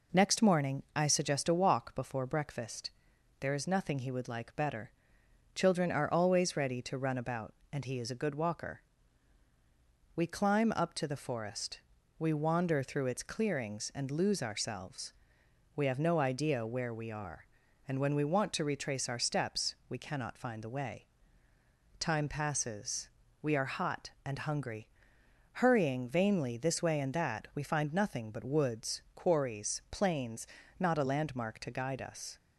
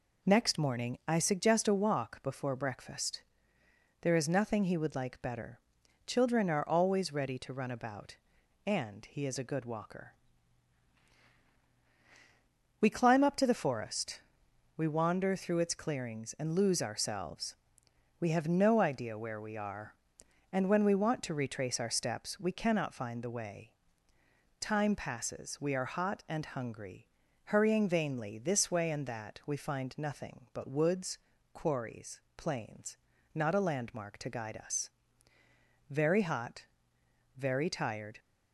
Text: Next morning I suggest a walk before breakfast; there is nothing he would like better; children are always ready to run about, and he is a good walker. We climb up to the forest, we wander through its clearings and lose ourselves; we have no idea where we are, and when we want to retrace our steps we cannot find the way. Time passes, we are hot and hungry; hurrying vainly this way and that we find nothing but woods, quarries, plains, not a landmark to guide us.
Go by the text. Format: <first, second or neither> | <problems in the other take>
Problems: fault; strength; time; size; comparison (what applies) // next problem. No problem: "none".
first | goes on to say "Very hot very tired"; strong; from 35.9 s on; 2.2 s long